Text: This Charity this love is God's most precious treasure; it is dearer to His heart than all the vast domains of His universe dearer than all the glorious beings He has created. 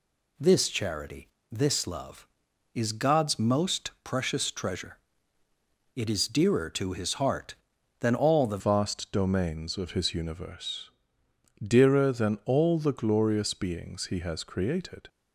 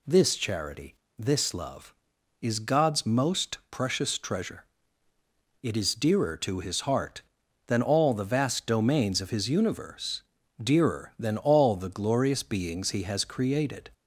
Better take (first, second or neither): second